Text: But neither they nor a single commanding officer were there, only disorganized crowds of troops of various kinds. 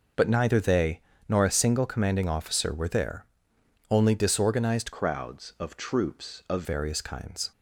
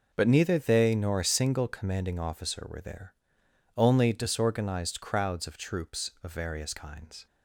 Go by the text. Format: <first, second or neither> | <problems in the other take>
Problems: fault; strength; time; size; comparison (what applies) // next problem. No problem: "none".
second | pauses between "they" and "nor"; slight; at 1.0 s; 0.28 s long // changes voice from "crowds" to "of"; from 4.9 to 6.6 s; 1.7 s long